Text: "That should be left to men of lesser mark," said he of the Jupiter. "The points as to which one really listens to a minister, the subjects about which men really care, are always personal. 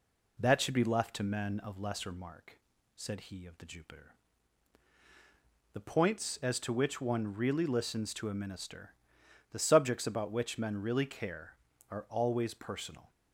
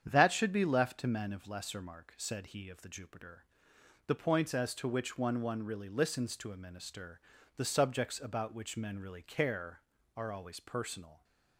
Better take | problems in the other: first | starts louder than the rest; strong; until 1.0 s; 8.5 dB // says "one" twice; at 5.3 s

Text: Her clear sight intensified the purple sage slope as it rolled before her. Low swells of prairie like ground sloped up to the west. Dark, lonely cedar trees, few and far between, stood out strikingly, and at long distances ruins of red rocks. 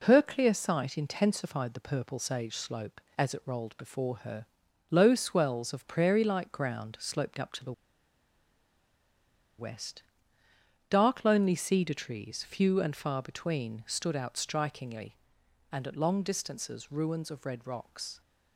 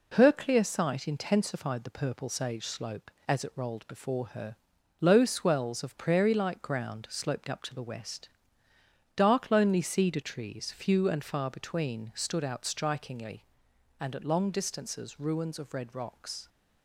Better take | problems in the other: second | pauses between "the" and "west"; strong; at 7.7 s; 1.8 s long

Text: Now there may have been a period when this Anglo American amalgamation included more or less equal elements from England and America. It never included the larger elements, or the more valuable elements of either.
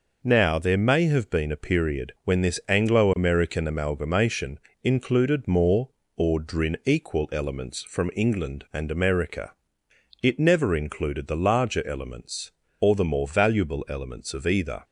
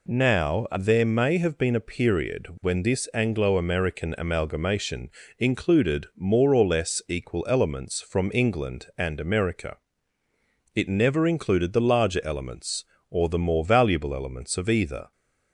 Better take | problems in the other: second | pauses between "amalgamation" and "included"; slight; at 4.5 s; 0.24 s long; slight in the second // says "drin" for "less"; at 6.3 s

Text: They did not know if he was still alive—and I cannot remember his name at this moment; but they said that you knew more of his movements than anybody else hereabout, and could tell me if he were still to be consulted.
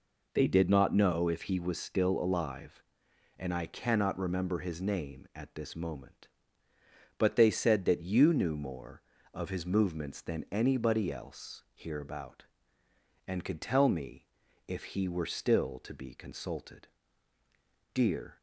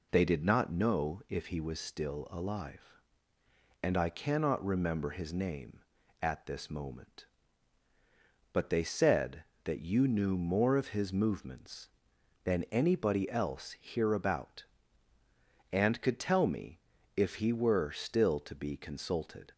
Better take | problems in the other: second | pauses between "me" and "if"; at 14.2 s; 0.40 s long; also in the second // goes on to say "Dear"; slight; from 17.9 s on; 0.44 s long

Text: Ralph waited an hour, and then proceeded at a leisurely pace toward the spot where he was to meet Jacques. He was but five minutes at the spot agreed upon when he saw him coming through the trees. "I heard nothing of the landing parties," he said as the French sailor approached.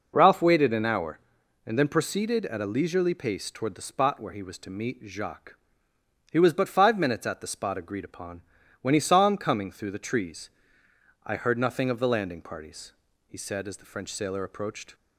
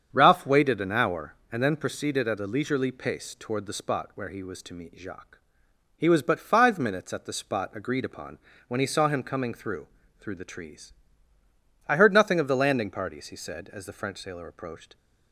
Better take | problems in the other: first | starts louder than the rest; strong; until 1.1 s; 7.5 dB // pauses between "upon" and "when"; slight; at 8.3 s; 0.28 s long; also in the first // says "through" twice; at 10.1 s

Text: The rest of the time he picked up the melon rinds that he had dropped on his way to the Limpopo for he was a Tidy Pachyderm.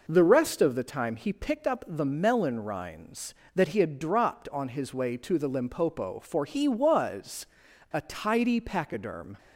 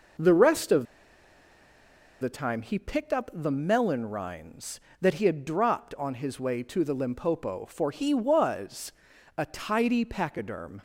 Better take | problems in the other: first | pauses between "of" and "the"; strong; at 0.8 s; 1.3 s long // pauses between "was" and "a"; noticeable; at 8.9 s; 0.46 s long; noticeable in the first

